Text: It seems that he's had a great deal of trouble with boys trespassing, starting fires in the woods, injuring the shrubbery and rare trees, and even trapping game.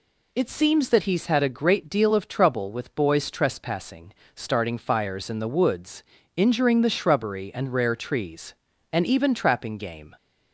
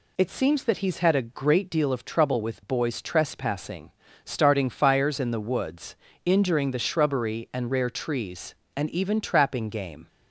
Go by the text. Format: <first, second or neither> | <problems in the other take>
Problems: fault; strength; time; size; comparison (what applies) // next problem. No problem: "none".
neither | none